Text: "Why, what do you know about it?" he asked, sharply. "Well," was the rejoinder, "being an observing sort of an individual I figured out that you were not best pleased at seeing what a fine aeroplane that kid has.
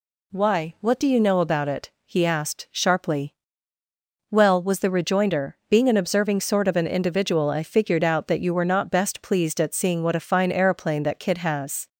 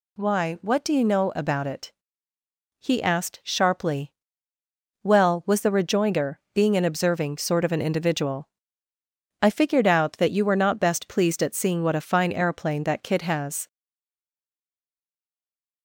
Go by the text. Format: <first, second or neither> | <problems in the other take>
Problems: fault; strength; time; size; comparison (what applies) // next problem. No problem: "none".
first | pauses between "individual" and "I"; noticeable; at 8.4 s; 0.94 s long // stays silent after the last word; from 13.6 s on; 2.2 s long